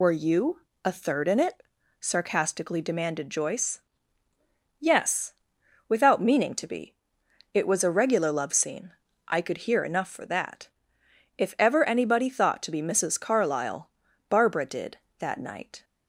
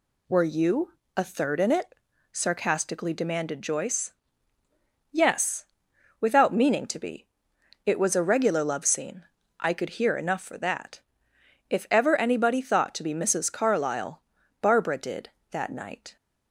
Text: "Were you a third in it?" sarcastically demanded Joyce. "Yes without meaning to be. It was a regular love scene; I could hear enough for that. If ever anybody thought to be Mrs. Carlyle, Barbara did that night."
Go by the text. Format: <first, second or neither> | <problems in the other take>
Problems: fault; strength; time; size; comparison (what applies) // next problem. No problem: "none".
second | loses the start of "Were"; at 0.0 s; 50 ms // pauses between "you" and "a"; slight; at 0.6 s; 0.22 s long; slight in the second // pauses between "Yes" and "without"; noticeable; at 5.3 s; 0.56 s long; noticeable in the second